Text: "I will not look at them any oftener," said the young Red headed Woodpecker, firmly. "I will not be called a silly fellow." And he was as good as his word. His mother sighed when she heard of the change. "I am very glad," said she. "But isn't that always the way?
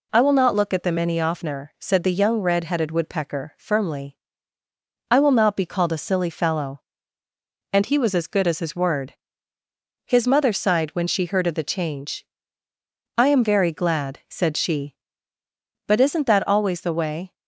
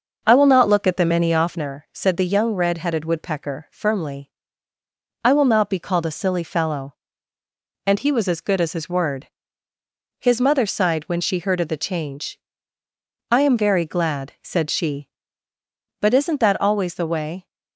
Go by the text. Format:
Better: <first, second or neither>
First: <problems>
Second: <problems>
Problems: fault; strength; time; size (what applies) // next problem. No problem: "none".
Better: first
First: none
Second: starts louder than the rest; noticeable; until 1.7 s; 6 dB